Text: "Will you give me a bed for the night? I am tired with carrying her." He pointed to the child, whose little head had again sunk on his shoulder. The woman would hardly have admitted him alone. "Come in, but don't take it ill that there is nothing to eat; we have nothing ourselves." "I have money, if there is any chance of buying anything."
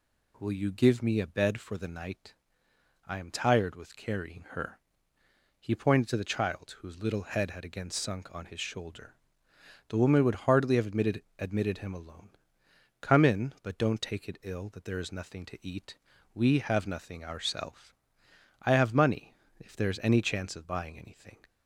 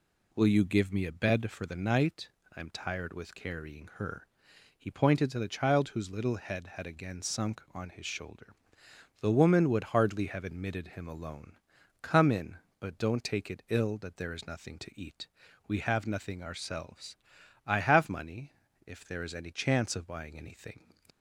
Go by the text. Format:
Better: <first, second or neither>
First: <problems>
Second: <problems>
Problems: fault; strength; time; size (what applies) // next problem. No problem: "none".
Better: second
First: says "admitted" twice; at 11.3 s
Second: none